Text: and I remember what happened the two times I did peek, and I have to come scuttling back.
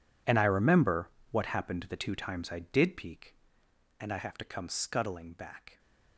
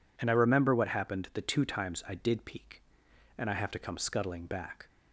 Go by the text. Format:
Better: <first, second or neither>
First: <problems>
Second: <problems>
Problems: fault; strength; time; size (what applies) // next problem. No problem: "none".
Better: second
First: gets quieter; strong; throughout; 17 dB // pauses between "remember" and "what"; slight; at 1.0 s; 0.22 s long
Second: none